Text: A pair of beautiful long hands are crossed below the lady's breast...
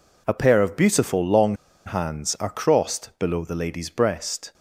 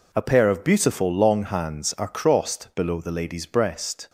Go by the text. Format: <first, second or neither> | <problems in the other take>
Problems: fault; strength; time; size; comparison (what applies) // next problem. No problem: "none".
second | pauses between "long" and "hands"; slight; at 1.5 s; 0.30 s long